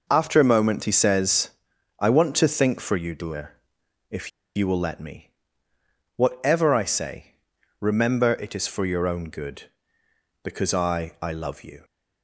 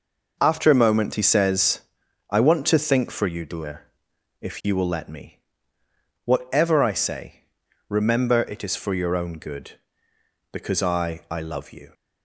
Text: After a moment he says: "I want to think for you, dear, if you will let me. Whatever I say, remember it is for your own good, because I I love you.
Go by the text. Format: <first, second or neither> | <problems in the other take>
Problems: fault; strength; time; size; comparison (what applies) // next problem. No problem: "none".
second | pauses between "if" and "you"; slight; at 4.3 s; 0.26 s long